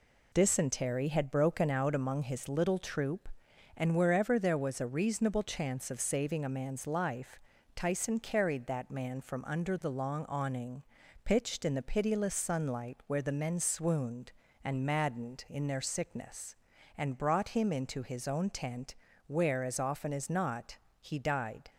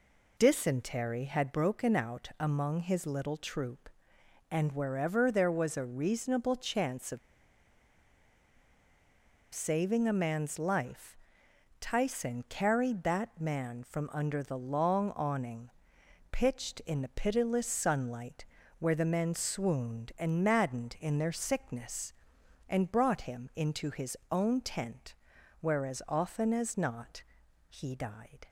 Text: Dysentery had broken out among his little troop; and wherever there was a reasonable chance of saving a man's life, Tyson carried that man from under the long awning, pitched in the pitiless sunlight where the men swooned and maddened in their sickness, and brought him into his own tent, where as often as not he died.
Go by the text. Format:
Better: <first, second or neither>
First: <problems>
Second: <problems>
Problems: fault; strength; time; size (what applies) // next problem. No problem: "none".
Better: first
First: pauses between "not" and "he"; slight; at 20.7 s; 0.22 s long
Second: pauses between "of" and "saving"; strong; at 7.1 s; 2.3 s long // pauses between "sunlight" and "where"; slight; at 18.4 s; 0.34 s long // pauses between "not" and "he"; noticeable; at 27.2 s; 0.46 s long